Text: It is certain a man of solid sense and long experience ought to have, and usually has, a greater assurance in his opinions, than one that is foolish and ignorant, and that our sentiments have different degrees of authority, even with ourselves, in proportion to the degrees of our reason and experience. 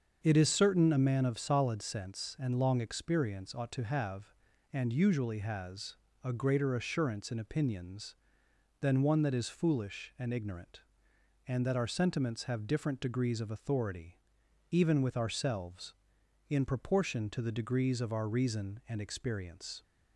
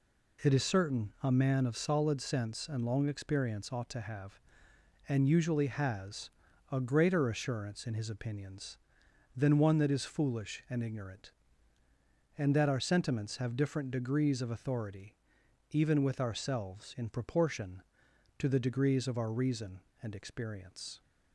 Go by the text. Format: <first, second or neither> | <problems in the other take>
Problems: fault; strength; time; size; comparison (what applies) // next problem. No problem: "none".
second | starts louder than the rest; until 1.2 s; 7 dB // skips "his"; at 7.3 s